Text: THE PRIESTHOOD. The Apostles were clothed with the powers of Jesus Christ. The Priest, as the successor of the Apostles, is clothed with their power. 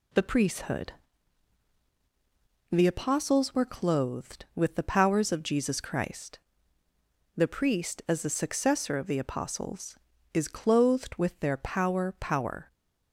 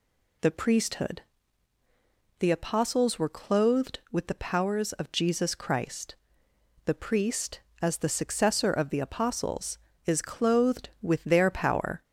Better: second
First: says "power" twice; at 12.1 s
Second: none

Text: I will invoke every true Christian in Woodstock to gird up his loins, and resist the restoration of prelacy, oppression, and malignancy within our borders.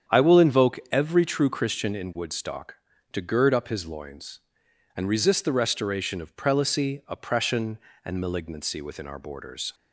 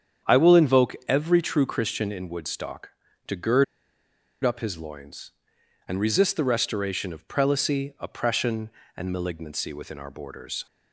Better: first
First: starts louder than the rest; strong; until 1.2 s; 8.5 dB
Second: starts louder than the rest; strong; until 1.3 s; 8.5 dB // pauses between "gird" and "up"; noticeable; at 3.6 s; 0.79 s long

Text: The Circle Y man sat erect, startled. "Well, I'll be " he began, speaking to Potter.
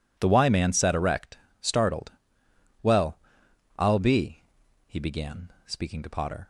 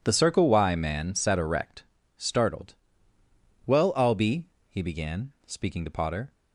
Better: second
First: skips "Circle"; at 0.2 s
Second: none

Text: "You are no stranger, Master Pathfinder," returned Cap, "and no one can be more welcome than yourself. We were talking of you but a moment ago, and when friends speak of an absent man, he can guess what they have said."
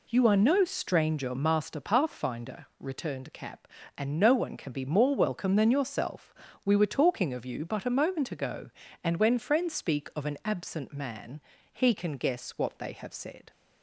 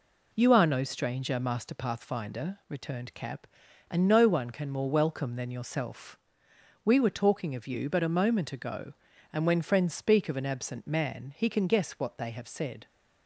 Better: first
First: none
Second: skips "be"; at 4.6 s

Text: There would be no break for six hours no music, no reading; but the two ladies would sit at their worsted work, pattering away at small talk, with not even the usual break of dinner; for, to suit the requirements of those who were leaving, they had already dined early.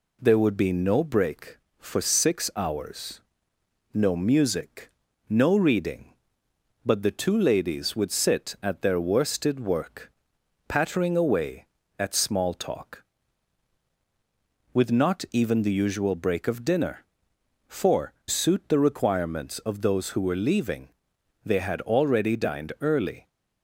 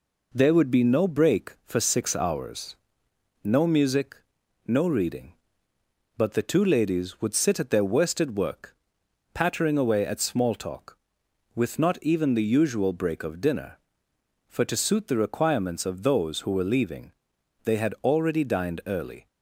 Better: second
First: pauses between "hours" and "no"; noticeable; at 3.2 s; 0.72 s long // skips "to"; at 18.2 s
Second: pauses between "hours" and "no"; noticeable; at 2.7 s; 0.68 s long

